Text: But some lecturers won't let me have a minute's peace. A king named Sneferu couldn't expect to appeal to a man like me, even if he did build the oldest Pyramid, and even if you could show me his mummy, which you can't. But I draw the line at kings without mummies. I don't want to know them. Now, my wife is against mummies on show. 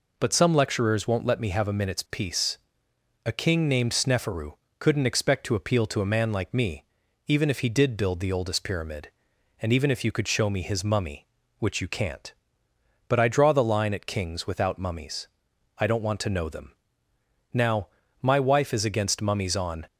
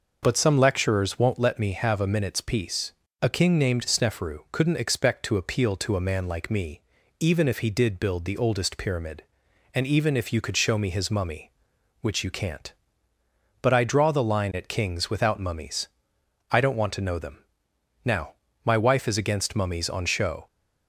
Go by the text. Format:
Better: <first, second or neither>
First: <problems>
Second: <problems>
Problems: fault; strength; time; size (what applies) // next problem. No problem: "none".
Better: second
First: pauses between "Sneferu" and "couldn't"; slight; at 4.5 s; 0.24 s long // stops before "show"; at 19.8 s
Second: none